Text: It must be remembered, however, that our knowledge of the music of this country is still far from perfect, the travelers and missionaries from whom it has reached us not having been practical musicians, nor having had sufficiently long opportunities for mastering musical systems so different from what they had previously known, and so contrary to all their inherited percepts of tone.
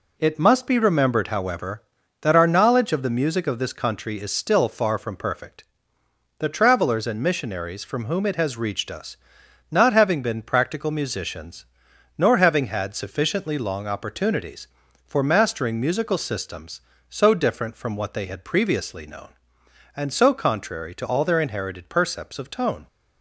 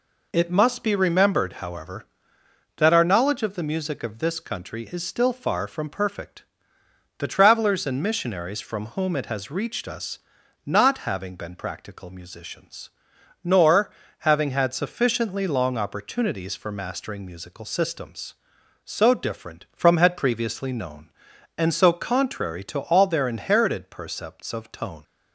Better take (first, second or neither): first